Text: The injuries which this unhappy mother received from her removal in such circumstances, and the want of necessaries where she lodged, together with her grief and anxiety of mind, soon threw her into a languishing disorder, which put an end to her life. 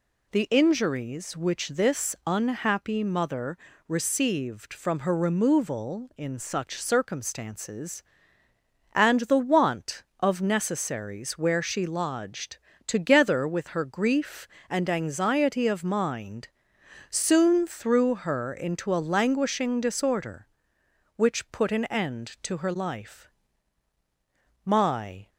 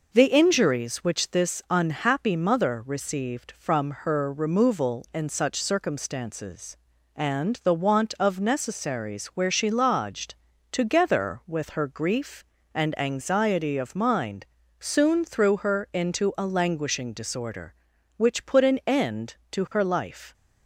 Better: second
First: pauses between "mother" and "received"; slight; at 3.5 s; 0.30 s long // goes on to say "My"; noticeable; from 24.6 s on; 0.66 s long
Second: none

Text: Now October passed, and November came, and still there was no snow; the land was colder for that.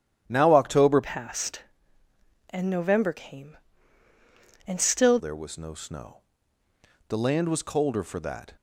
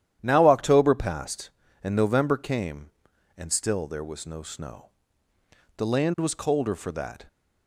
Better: second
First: starts louder than the rest; strong; until 1.2 s; 11 dB // changes voice from "passed" to "still"; from 1.0 to 5.1 s; 4.1 s long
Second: starts louder than the rest; strong; until 1.2 s; 11 dB

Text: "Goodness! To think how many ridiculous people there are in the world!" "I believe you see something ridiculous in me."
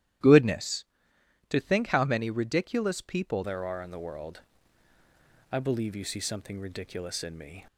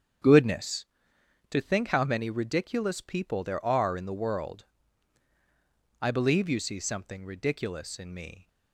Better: second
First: starts louder than the rest; strong; until 1.8 s; 12 dB // changes voice at "there"; from 3.4 s on; 4.2 s long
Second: starts louder than the rest; strong; until 1.8 s; 8 dB

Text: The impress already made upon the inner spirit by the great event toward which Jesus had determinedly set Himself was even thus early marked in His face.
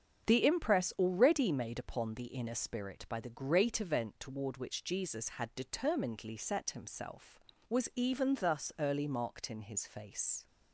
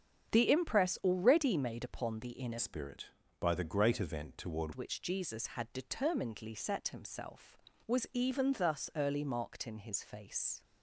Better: first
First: starts louder than the rest; strong; until 1.3 s; 7.5 dB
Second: starts louder than the rest; strong; until 1.3 s; 8 dB // changes voice from "spirit" to "toward"; from 2.5 to 4.7 s; 2.2 s long

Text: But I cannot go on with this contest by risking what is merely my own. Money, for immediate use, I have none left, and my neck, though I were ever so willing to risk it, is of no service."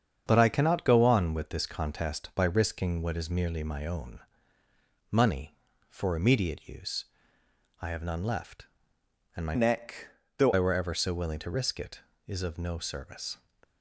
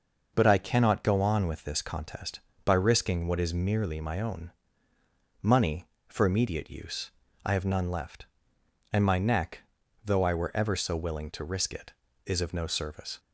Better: second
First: starts louder than the rest; strong; until 1.2 s; 7.5 dB // changes voice from "neck" to "though"; from 9.5 to 10.5 s; 1.0 s long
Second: none

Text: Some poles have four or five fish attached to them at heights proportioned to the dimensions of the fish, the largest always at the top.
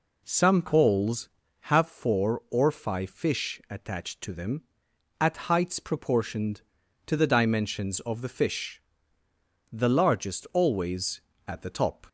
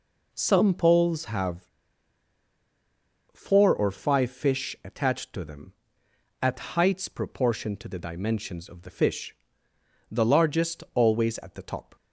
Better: first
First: none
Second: pauses between "have" and "four"; strong; at 1.6 s; 1.6 s long

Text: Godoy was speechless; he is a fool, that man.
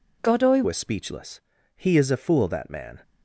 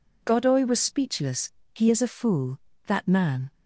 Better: second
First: changes voice at "was"; from 0.6 s on; 2.4 s long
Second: none

